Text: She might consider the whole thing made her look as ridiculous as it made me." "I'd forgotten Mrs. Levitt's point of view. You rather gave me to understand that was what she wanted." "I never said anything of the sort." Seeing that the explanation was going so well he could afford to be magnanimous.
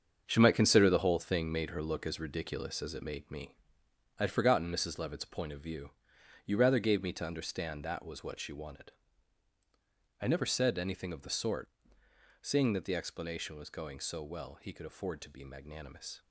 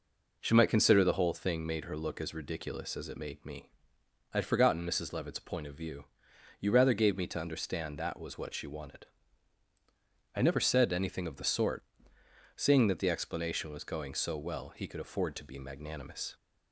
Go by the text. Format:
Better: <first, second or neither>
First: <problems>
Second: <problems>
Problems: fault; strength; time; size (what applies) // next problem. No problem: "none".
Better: second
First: gets quieter; strong; throughout; 9 dB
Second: none